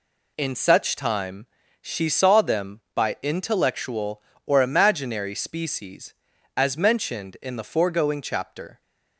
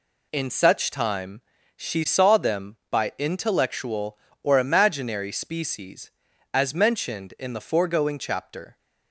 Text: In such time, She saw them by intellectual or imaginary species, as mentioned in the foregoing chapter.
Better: neither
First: none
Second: none

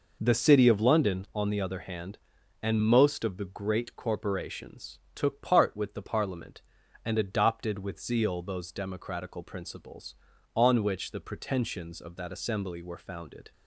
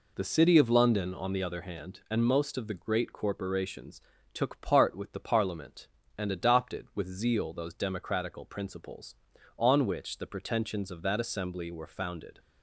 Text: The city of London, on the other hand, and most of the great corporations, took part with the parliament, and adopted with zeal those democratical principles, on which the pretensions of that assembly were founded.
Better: neither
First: none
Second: none

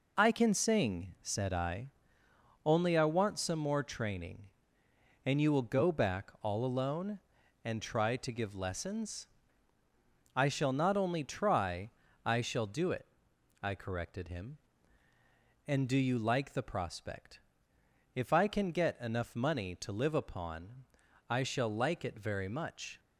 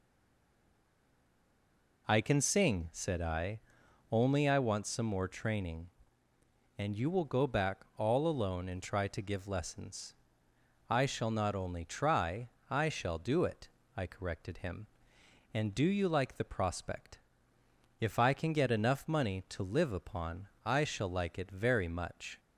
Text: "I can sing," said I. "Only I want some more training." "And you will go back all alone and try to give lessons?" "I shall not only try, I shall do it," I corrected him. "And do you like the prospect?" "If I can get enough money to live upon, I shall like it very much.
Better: first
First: none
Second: stays silent before the first word; noticeable; until 2.0 s; 2.0 s long

